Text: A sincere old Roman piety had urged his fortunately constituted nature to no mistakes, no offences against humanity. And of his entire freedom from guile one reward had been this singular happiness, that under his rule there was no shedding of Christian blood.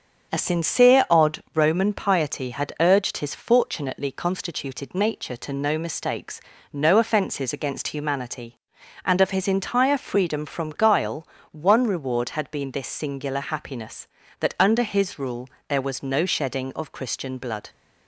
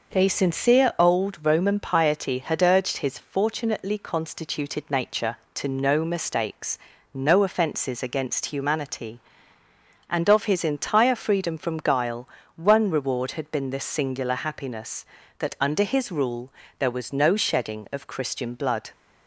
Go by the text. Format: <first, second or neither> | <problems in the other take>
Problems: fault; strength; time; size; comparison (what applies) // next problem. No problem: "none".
second | starts louder than the rest; until 1.3 s; 6.5 dB // says "odd" for "old"; at 1.1 s // pauses between "guile" and "one"; slight; at 11.2 s; 0.24 s long; slight in the second // pauses between "rule" and "there"; slight; at 15.4 s; 0.18 s long; slight in the second